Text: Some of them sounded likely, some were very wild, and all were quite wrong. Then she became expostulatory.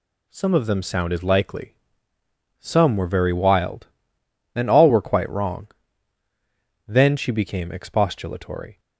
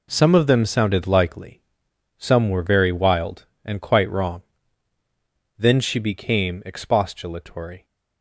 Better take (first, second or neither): first